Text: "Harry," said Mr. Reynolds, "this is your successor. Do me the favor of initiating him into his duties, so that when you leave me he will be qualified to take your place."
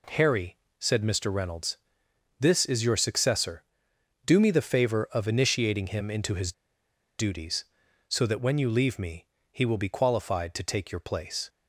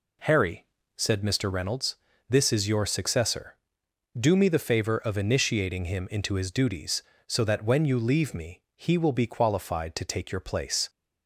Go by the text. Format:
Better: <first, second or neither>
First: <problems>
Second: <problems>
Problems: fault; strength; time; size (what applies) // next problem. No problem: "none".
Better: second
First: pauses between "his" and "duties"; noticeable; at 6.5 s; 0.65 s long // pauses between "me" and "he"; slight; at 9.2 s; 0.24 s long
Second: none